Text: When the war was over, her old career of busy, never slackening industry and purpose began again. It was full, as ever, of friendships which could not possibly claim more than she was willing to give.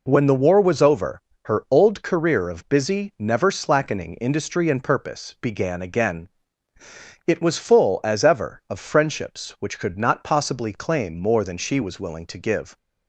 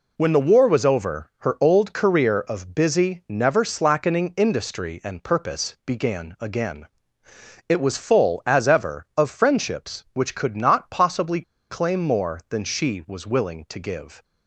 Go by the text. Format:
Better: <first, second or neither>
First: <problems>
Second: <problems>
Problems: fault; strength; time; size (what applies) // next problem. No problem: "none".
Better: first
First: none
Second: pauses between "possibly" and "claim"; slight; at 11.4 s; 0.27 s long